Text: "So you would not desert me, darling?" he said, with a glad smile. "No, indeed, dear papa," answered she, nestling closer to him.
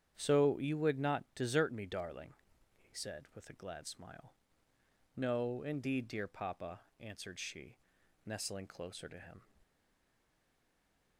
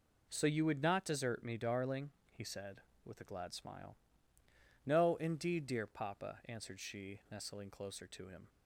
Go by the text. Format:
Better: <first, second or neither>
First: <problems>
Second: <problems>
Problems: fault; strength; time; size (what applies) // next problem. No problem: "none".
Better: second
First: starts louder than the rest; strong; until 1.1 s; 9 dB // stays silent after the last word; noticeable; from 9.6 s on; 1.5 s long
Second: none